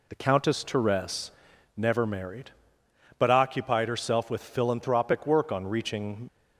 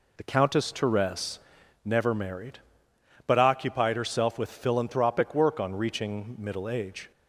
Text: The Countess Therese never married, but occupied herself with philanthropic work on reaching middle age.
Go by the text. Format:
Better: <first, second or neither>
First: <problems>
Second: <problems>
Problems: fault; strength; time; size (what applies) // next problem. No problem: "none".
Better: second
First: pauses between "Therese" and "never"; noticeable; at 1.3 s; 0.46 s long // stops before "middle age"; at 6.2 s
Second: pauses between "Therese" and "never"; noticeable; at 1.3 s; 0.46 s long